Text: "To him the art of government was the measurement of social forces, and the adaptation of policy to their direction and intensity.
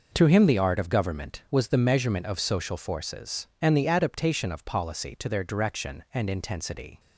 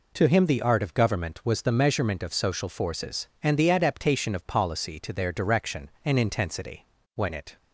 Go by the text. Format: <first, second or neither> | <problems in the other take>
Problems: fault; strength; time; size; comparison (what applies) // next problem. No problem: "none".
first | goes on to say "When it"; slight; from 7.1 s on; 0.42 s long